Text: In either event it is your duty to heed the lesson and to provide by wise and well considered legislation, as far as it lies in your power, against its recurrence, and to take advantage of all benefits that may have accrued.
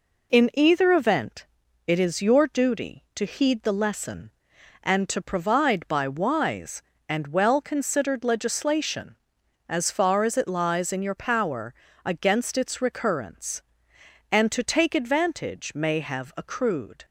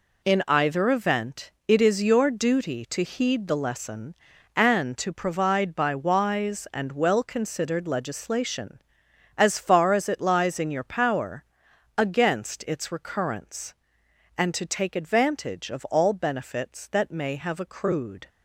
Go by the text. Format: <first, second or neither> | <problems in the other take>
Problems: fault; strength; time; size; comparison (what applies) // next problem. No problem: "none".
second | pauses between "event" and "it"; at 1.4 s; 0.42 s long; slight in the second // skips "of all benefits that"; at 15.7 s